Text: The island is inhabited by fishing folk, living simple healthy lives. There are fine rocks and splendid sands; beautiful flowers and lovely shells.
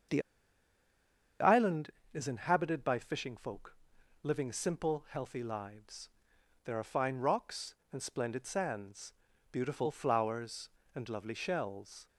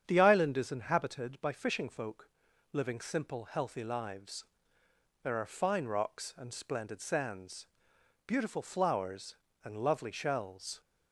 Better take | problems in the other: second | starts louder than the rest; strong; until 2.5 s; 7 dB; strong in the second // pauses between "The" and "island"; at 0.2 s; 1.1 s long

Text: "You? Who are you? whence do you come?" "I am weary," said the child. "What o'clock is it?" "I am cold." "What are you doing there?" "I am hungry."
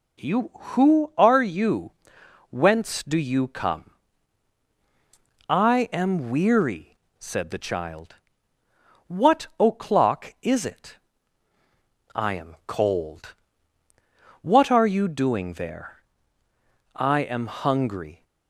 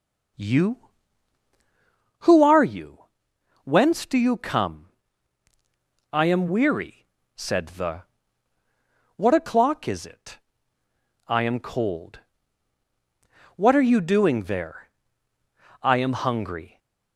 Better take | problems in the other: first | skips "child"; at 8.6 s

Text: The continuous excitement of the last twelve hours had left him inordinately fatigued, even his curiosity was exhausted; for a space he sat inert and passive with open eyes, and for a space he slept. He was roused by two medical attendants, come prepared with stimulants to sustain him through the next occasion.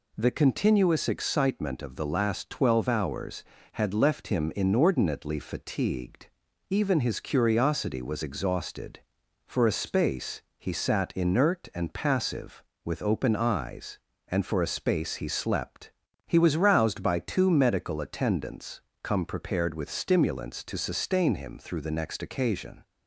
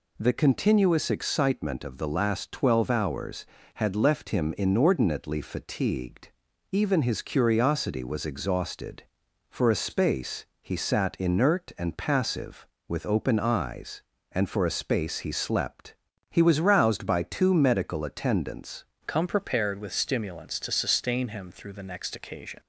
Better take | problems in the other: first | pauses between "space" and "he"; slight; at 10.4 s; 0.16 s long; slight in the first // changes voice at "come"; from 19.0 s on; 3.5 s long

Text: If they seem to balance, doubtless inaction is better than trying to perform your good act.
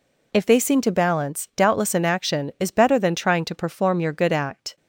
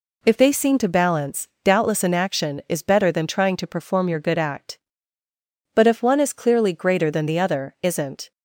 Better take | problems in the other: first | goes on to say "But if one is clearly greater than the other isn't"; strong; from 5.7 s on; 2.5 s long

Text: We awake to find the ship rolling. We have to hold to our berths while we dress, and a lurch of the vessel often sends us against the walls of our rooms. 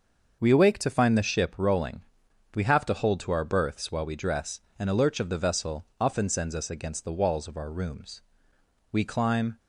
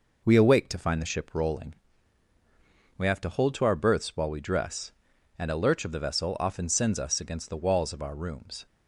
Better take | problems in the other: second | starts louder than the rest; until 1.4 s; 6 dB // goes on to say "We climb"; noticeable; from 8.9 s on; 0.66 s long

